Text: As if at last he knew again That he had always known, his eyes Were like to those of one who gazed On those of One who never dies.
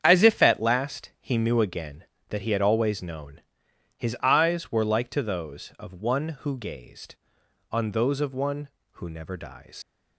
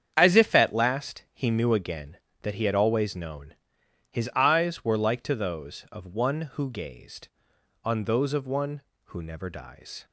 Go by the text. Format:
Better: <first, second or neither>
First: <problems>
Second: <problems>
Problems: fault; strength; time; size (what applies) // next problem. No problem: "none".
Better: second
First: starts louder than the rest; strong; until 1.0 s; 8.5 dB // leaves "dies" unfinished; at 9.8 s; 100 ms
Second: starts louder than the rest; strong; until 1.1 s; 8.5 dB